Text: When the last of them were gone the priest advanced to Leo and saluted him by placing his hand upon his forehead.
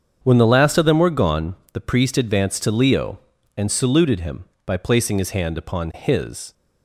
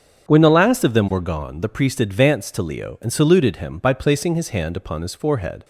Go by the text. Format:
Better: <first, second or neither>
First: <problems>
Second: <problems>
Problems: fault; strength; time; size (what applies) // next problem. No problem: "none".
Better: second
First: starts louder than the rest; strong; until 1.2 s; 7.5 dB // pauses between "gone" and "the"; slight; at 1.5 s; 0.18 s long // stops before "forehead"; at 6.5 s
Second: starts louder than the rest; until 1.3 s; 7 dB